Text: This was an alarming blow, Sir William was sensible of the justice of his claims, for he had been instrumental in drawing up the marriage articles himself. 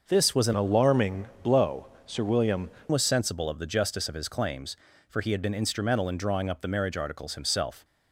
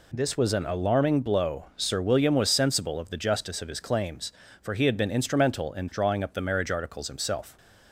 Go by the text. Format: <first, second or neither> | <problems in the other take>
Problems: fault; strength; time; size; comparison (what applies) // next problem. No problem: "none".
second | starts louder than the rest; until 1.1 s; 6 dB // changes voice from "alarming" to "William"; from 0.5 to 2.7 s; 2.2 s long // pauses between "alarming" and "blow"; slight; at 1.2 s; 0.16 s long